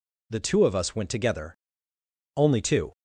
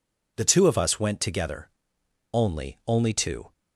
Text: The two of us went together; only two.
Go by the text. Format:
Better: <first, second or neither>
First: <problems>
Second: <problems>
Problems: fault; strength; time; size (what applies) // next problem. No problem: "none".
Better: first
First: none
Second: says "only" twice; at 2.8 s